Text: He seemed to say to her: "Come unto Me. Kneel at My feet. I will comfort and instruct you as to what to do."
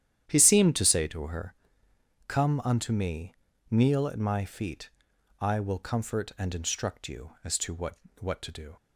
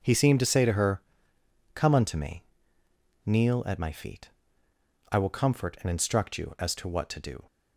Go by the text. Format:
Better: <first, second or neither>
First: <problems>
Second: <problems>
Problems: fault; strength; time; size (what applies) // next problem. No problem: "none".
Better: second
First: starts louder than the rest; strong; until 1.3 s; 10 dB // says "what" twice; at 8.1 s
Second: none